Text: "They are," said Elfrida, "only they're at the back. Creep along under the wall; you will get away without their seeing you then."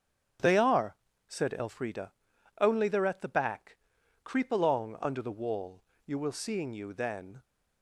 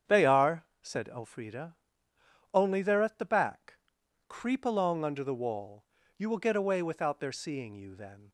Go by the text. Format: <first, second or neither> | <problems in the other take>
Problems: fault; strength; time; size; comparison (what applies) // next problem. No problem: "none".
second | starts louder than the rest; strong; until 1.7 s; 9 dB; strong in the second // skips "get away without their"; at 6.3 s